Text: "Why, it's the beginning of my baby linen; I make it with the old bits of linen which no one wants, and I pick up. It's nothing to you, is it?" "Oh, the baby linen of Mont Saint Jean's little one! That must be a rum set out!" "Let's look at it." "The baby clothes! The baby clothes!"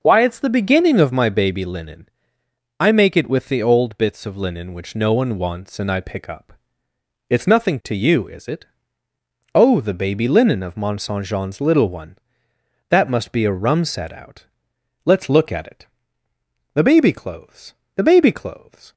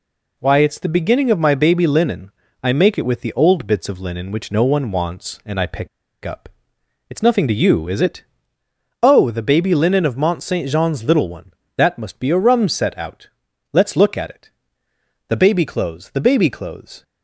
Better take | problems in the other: first | pauses between "pick" and "up"; at 5.8 s; 0.36 s long

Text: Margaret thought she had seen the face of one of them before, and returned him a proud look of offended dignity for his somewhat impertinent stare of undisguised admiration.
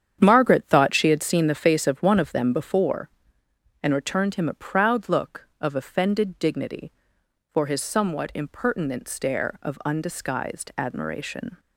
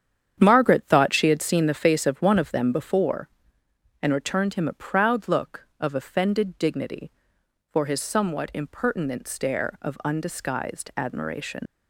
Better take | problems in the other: first | starts louder than the rest; strong; until 1.4 s; 8.5 dB; strong in the first // leaves "admiration" unfinished; at 11.6 s; 130 ms

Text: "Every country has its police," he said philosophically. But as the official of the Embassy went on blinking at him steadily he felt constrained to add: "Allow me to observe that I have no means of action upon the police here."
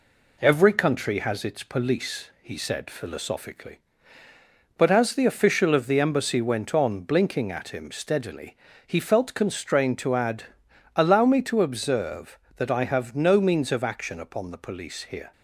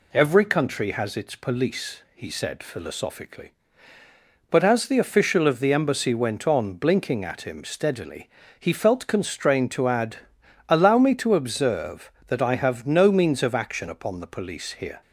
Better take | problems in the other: second | gets quieter; slight; throughout; 2.5 dB // pauses between "steadily" and "he"; slight; at 8.5 s; 0.30 s long; slight in the second

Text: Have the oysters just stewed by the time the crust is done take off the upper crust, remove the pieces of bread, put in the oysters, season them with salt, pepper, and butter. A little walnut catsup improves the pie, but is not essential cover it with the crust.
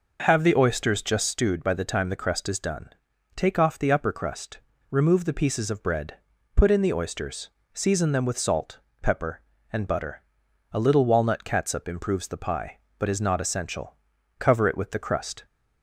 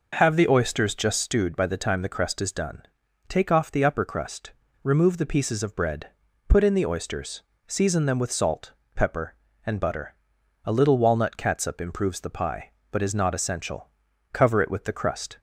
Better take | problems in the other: neither | pauses between "done" and "take"; the same in both // pauses between "essential" and "cover"; the same in both

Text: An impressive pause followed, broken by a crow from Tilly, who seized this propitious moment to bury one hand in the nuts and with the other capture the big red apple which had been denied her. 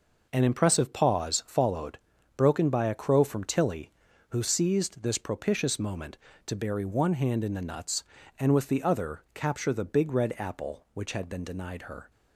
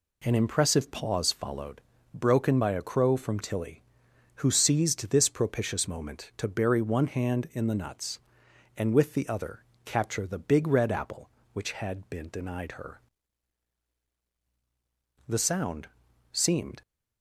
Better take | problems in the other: first | pauses between "other" and "capture"; slight; at 9.6 s; 0.22 s long // goes on to say "The sound seemed"; from 15.2 s on; 1.5 s long

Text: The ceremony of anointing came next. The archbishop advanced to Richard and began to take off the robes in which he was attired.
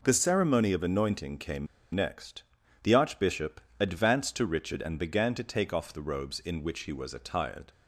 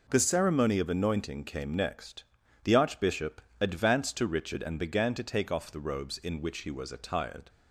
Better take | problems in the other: second | pauses between "came" and "next"; slight; at 1.6 s; 0.27 s long // pauses between "archbishop" and "advanced"; slight; at 3.6 s; 0.18 s long; slight in the second

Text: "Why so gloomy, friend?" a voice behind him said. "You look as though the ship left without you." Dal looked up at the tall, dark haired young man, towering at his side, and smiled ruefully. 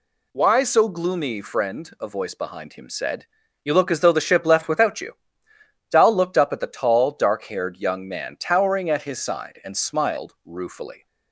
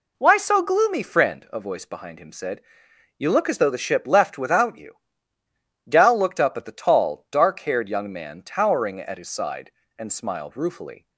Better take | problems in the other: neither | none

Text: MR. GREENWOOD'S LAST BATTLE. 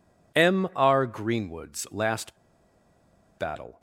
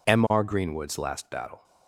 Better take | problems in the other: second | pauses between "LAST" and "BATTLE"; at 2.3 s; 1.0 s long

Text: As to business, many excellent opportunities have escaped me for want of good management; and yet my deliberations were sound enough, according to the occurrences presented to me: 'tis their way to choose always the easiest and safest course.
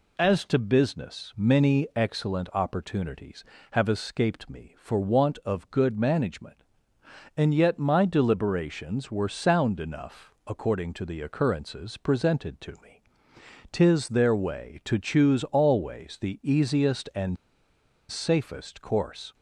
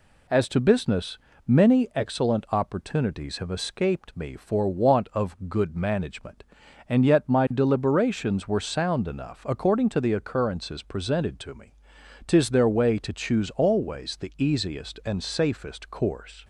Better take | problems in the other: second | pauses between "and" and "safest"; noticeable; at 17.3 s; 0.73 s long

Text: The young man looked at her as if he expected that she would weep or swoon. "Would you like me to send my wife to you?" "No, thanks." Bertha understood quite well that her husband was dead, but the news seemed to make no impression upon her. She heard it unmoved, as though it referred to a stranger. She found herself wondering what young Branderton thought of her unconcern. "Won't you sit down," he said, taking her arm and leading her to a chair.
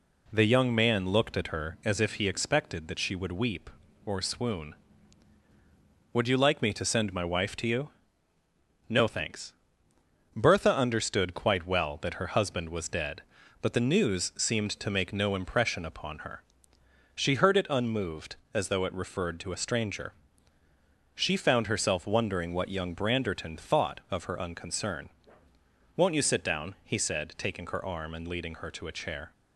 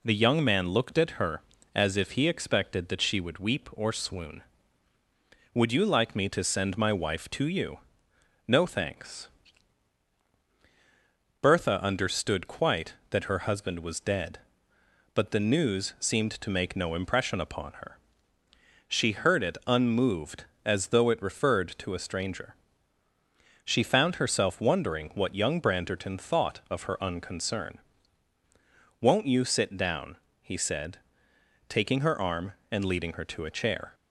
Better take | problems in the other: first | skips "well"; at 13.0 s

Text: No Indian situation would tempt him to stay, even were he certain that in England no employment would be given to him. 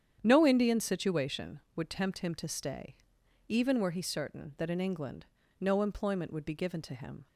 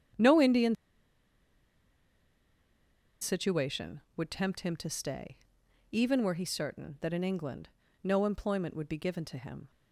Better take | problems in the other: first | starts louder than the rest; strong; until 3.6 s; 9 dB; strong in the first // pauses between "Indian" and "situation"; strong; at 0.7 s; 2.4 s long // pauses between "England" and "no"; slight; at 7.6 s; 0.34 s long; slight in the first

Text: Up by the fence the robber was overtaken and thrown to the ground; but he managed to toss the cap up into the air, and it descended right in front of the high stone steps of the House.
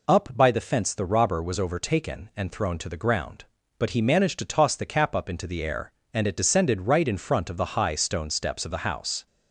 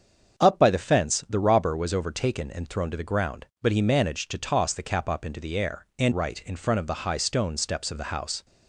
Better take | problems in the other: first | starts louder than the rest; until 1.4 s; 7 dB // skips "it descended"; at 6.1 s

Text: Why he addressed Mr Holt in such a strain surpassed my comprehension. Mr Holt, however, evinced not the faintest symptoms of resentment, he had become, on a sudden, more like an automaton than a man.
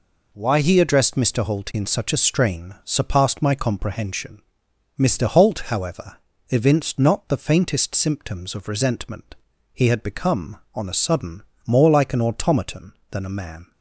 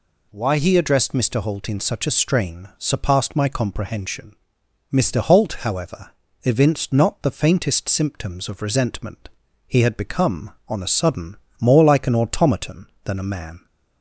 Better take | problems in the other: second | gets quieter; strong; throughout; 7 dB

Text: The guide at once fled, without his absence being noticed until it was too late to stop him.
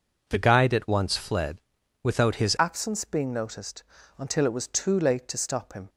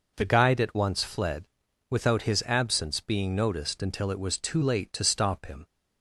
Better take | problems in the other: second | changes voice at "absence"; from 2.5 s on; 3.3 s long // pauses between "noticed" and "until"; slight; at 3.8 s; 0.34 s long

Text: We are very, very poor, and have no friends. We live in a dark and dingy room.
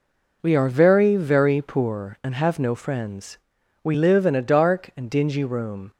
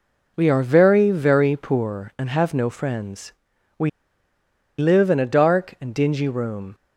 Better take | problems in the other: first | pauses between "We" and "live"; noticeable; at 3.8 s; 0.88 s long

